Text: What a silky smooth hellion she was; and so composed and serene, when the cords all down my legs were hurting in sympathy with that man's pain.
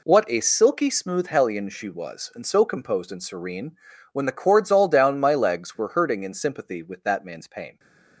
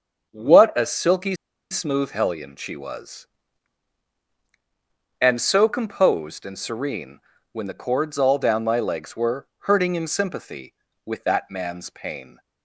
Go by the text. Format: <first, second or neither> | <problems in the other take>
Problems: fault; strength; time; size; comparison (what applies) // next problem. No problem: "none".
first | starts louder than the rest; until 1.3 s; 6.5 dB // pauses between "silky" and "smooth"; at 1.3 s; 0.37 s long